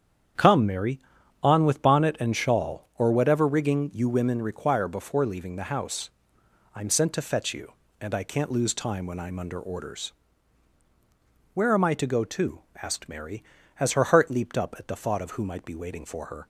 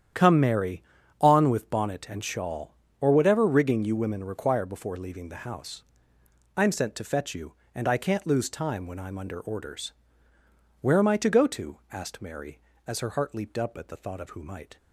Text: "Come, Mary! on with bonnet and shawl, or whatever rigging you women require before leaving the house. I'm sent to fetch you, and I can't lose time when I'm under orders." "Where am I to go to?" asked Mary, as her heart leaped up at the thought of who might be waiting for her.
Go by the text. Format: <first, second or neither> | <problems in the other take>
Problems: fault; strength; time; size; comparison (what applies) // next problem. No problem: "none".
first | starts louder than the rest; strong; until 1.5 s; 10 dB; strong in the first // stops before "be waiting for her"; at 14.7 s